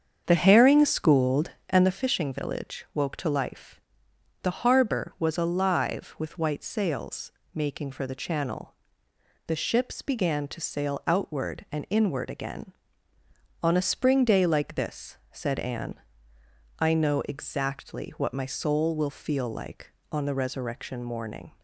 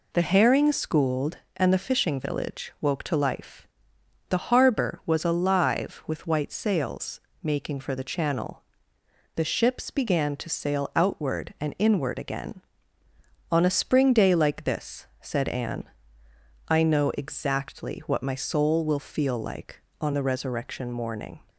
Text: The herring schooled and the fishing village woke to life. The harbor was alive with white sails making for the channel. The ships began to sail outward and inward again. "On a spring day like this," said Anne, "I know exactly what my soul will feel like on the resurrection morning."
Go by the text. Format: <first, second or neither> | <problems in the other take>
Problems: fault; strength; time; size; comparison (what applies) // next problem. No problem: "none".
second | starts louder than the rest; strong; until 1.9 s; 7.5 dB // pauses between "sails" and "making"; slight; at 7.3 s; 0.24 s long; slight in the second